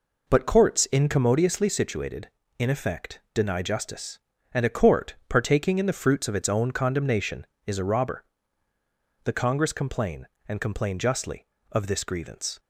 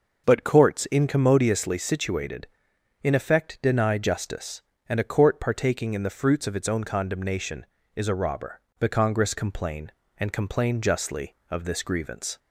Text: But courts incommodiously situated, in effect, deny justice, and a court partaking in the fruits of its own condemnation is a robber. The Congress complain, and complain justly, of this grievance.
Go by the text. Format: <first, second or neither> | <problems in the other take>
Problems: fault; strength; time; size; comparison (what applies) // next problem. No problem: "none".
neither | none